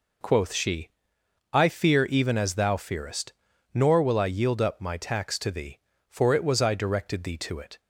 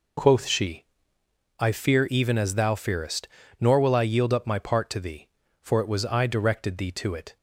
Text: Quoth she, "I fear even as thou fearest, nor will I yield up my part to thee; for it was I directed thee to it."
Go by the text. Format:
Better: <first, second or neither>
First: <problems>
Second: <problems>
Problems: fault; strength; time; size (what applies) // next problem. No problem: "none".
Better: second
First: says "tax" for "part"; at 4.9 s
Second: none